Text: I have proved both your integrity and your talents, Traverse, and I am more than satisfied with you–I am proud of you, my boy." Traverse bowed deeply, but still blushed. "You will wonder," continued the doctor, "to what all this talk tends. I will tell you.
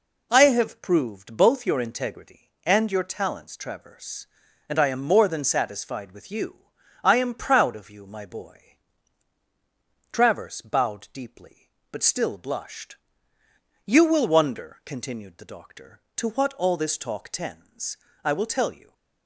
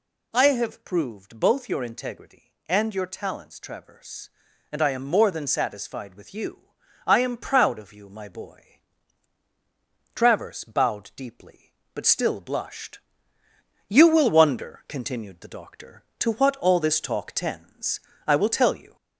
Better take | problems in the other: first | gets louder; slight; throughout; 2 dB

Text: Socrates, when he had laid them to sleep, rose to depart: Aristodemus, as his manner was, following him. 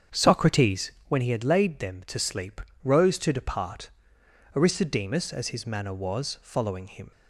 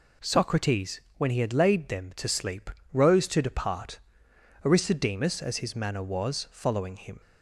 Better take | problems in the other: second | starts louder than the rest; strong; until 1.3 s; 7.5 dB

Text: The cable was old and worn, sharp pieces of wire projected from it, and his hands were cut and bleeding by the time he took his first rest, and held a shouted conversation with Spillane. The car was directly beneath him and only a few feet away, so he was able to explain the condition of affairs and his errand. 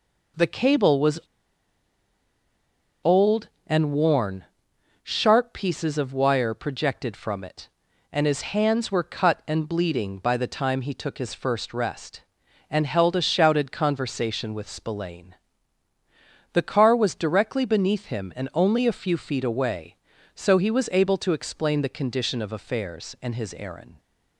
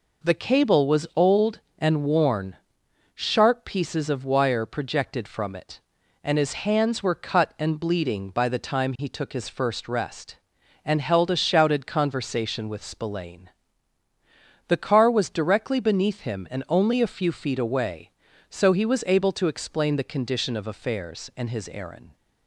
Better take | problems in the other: second | pauses between "was" and "old"; strong; at 1.1 s; 1.8 s long

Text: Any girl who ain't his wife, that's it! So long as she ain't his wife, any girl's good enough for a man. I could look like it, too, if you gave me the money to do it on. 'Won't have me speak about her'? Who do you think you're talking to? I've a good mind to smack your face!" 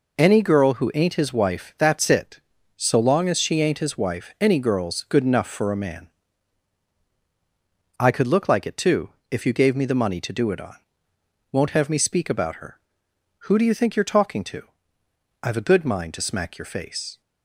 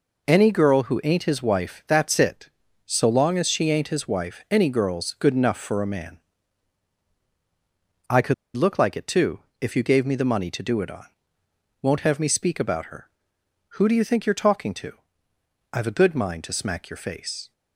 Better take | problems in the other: first | pauses between "could" and "look"; slight; at 8.3 s; 0.21 s long

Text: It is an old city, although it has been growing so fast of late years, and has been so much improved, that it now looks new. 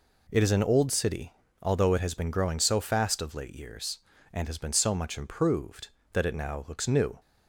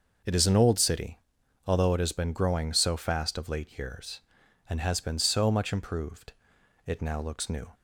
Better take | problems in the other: first | starts louder than the rest; until 1.7 s; 6 dB // skips "that"; at 6.5 s

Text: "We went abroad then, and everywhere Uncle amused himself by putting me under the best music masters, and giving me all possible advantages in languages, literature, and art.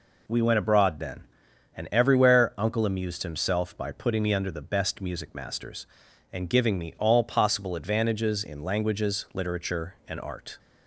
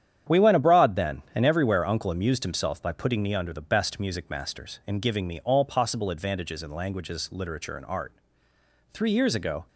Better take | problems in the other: first | starts louder than the rest; strong; until 1.4 s; 9.5 dB // goes on to say "Three years ago"; noticeable; from 8.9 s on; 0.76 s long

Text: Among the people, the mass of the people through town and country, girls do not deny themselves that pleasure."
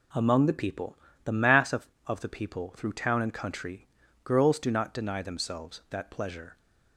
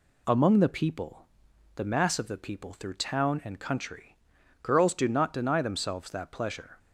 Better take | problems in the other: second | says "of" twice; at 2.0 s

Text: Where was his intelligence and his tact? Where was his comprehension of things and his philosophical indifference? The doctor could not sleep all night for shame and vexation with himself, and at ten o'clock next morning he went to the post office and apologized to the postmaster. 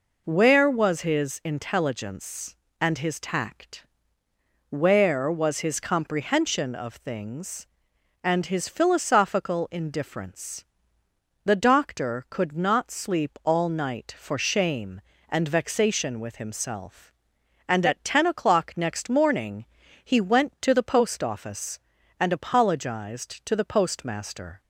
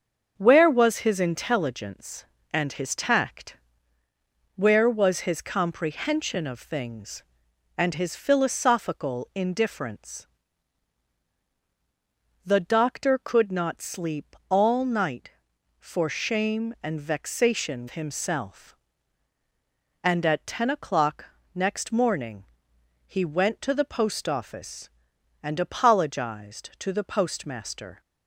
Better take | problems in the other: first | starts louder than the rest; until 1.3 s; 6.5 dB // skips "with"; at 17.8 s // pauses between "o'clock" and "next"; slight; at 21.2 s; 0.28 s long // pauses between "morning" and "he"; noticeable; at 22.4 s; 0.62 s long; also in the first

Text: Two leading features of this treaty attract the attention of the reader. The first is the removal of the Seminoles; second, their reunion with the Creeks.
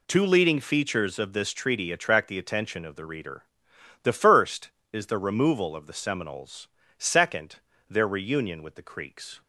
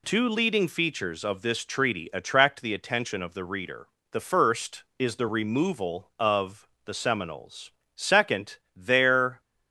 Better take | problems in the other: first | pauses between "of" and "the"; slight; at 6.6 s; 0.16 s long // stops before "reunion with the Creeks"; at 9.3 s

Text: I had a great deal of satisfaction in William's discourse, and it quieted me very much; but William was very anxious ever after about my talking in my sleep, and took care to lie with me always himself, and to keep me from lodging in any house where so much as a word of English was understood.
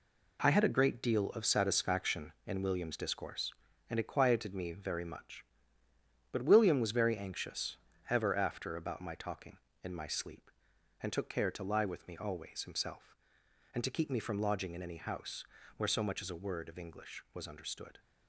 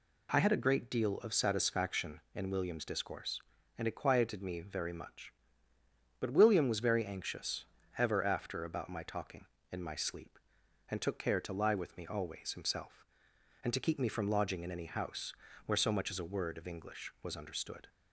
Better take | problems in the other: second | gets quieter; strong; throughout; 8 dB // pauses between "anxious" and "ever"; slight; at 7.7 s; 0.32 s long; slight in the second // pauses between "house" and "where"; slight; at 15.4 s; 0.32 s long; slight in the second

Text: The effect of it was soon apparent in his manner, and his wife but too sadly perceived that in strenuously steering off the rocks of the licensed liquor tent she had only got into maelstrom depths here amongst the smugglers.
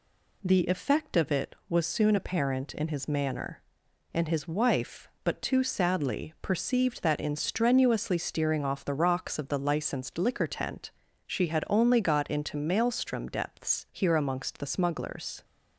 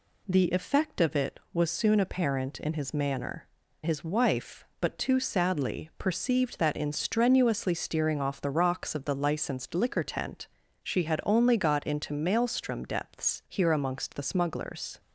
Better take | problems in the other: first | skips "and"; at 3.6 s // pauses between "tent" and "she"; slight; at 10.4 s; 0.34 s long; slight in the first

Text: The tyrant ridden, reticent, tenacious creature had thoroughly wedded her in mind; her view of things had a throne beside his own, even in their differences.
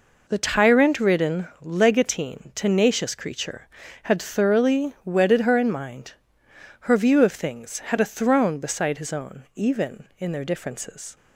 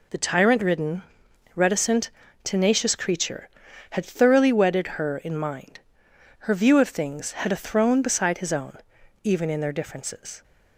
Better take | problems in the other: second | says "legatine" for "reticent"; at 1.6 s

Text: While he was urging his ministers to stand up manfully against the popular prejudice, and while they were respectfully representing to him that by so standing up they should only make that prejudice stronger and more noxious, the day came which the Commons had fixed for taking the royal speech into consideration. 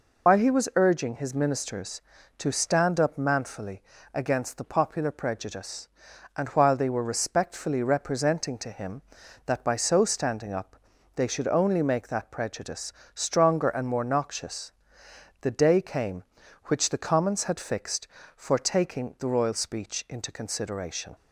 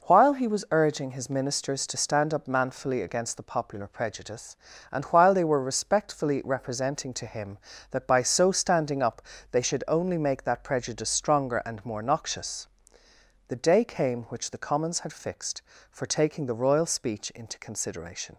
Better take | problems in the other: second | loses the start of "While"; at 0.2 s; 60 ms // pauses between "manfully" and "against"; slight; at 3.8 s; 0.30 s long // pauses between "up" and "they"; at 10.7 s; 0.40 s long; slight in the second // pauses between "prejudice" and "stronger"; slight; at 12.9 s; 0.22 s long

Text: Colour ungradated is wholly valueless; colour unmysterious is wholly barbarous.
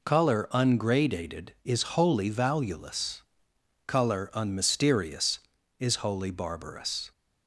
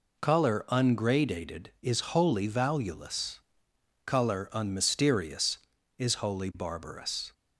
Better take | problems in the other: neither | none

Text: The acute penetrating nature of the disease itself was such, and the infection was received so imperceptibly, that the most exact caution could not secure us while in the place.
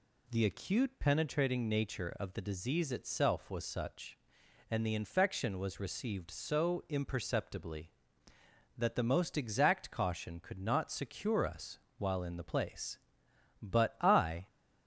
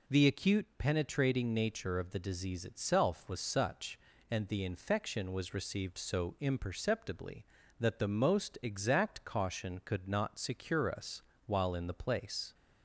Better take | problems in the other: second | pauses between "us" and "while"; slight; at 11.7 s; 0.20 s long; slight in the second // goes on to say "But I"; noticeable; from 13.6 s on; 0.84 s long

